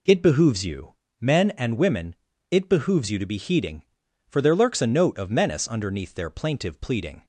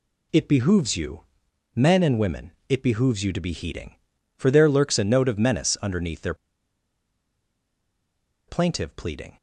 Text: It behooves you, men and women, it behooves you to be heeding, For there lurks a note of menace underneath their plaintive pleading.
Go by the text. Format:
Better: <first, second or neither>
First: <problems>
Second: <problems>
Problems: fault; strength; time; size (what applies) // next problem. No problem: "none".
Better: first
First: none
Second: pauses between "their" and "plaintive"; strong; at 6.3 s; 2.1 s long